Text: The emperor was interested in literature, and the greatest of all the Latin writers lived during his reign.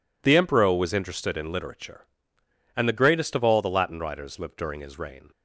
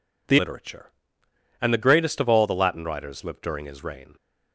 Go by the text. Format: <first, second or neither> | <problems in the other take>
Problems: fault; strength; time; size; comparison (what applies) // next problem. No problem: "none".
first | skips "emperor was interested in"; at 0.3 s